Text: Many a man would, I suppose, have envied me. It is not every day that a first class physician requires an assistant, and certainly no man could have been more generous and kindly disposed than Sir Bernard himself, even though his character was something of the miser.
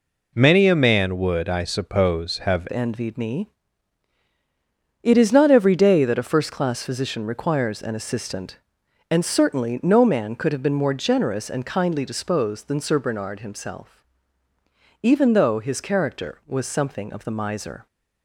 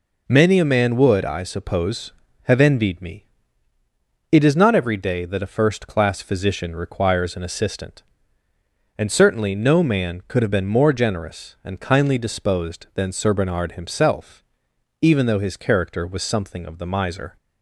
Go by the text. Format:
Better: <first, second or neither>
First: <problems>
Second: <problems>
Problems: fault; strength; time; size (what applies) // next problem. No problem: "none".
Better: second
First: changes voice at "envied"; from 2.7 s on; 15.1 s long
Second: none